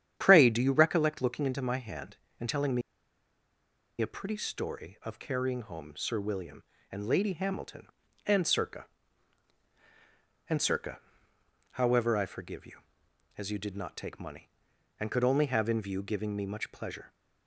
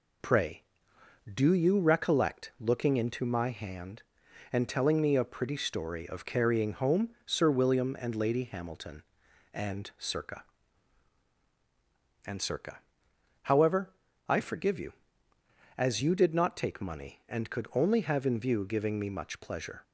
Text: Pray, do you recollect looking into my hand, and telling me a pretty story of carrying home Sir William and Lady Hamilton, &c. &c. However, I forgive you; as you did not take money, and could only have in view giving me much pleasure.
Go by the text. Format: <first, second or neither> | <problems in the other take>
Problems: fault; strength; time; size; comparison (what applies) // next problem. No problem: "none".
second | starts louder than the rest; strong; until 1.1 s; 9.5 dB // pauses between "me" and "a"; at 2.8 s; 1.1 s long